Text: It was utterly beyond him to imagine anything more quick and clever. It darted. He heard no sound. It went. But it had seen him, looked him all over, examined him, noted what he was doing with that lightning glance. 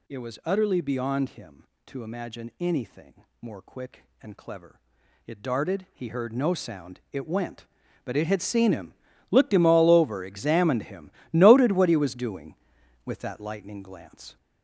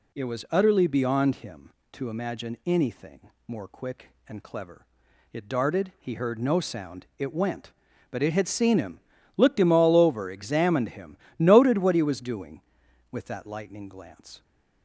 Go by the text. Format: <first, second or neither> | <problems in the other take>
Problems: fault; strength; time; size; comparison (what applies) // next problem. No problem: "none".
second | gets louder; noticeable; throughout; 5.5 dB // pauses between "anything" and "more"; slight; at 3.2 s; 0.18 s long; slight in the second